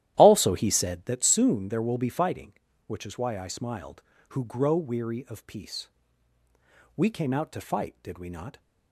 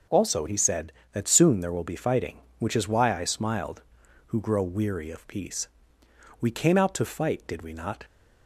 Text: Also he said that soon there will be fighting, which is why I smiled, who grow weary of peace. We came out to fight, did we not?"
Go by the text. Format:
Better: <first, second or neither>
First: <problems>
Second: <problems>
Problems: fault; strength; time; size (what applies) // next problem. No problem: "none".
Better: second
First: starts louder than the rest; strong; until 1.2 s; 13 dB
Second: none